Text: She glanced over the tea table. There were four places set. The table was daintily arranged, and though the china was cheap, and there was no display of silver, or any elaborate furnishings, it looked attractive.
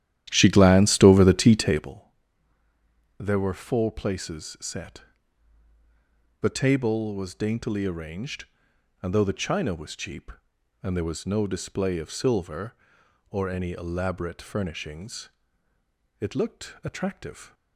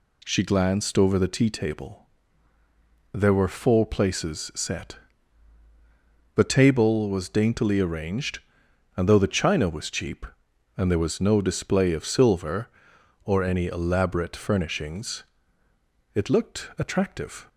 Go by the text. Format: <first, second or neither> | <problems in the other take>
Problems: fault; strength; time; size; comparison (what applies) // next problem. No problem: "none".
second | starts louder than the rest; strong; until 2.0 s; 12 dB